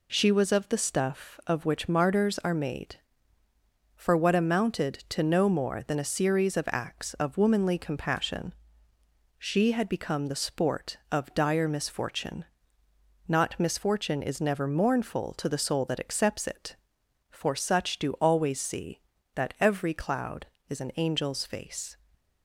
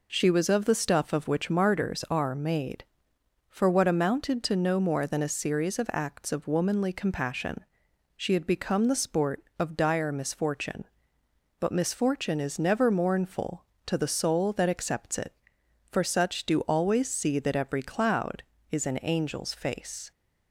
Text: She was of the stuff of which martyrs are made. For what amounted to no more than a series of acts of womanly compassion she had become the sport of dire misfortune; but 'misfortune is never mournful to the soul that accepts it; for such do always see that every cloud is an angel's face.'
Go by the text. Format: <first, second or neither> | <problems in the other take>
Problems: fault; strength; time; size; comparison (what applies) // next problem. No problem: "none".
second | pauses between "compassion" and "she"; noticeable; at 8.5 s; 0.86 s long; noticeable in the second // says "not" for "but"; at 13.2 s